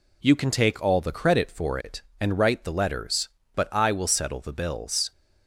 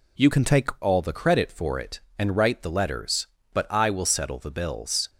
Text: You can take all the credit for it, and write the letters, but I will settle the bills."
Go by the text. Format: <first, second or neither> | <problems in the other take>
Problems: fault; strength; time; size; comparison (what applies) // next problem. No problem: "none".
first | changes voice from "can" to "take"; from 0.3 to 0.6 s; 0.3 s long